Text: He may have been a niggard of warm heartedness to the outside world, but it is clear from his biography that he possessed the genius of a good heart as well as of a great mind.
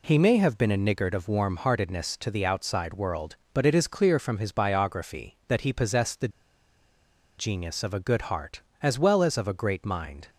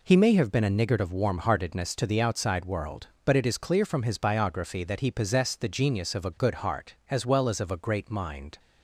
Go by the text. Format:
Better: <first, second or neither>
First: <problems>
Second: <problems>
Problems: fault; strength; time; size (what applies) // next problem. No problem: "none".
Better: second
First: pauses between "the" and "genius"; at 6.2 s; 1.0 s long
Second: none